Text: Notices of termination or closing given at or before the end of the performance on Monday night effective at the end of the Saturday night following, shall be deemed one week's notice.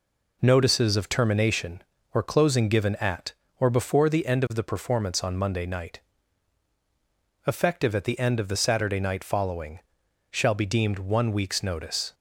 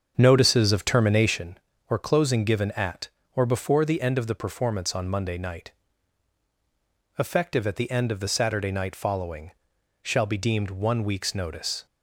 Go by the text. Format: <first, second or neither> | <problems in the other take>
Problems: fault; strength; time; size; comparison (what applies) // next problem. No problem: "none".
first | starts louder than the rest; strong; until 1.4 s; 7 dB // pauses between "night" and "effective"; strong; at 5.7 s; 1.4 s long; strong in the first